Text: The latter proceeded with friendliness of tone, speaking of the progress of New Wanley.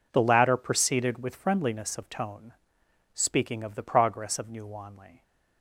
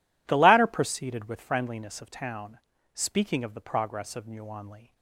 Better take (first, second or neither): first